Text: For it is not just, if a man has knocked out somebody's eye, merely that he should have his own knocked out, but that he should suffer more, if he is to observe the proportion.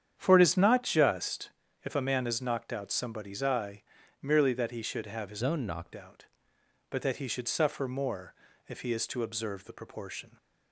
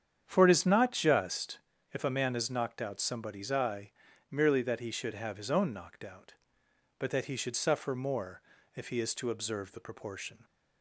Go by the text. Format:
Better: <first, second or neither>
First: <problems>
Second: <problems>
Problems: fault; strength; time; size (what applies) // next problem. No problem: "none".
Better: second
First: starts louder than the rest; strong; until 1.1 s; 9 dB // changes voice from "own" to "knocked"; from 5.4 to 5.9 s; 0.5 s long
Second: starts louder than the rest; strong; until 1.2 s; 8.5 dB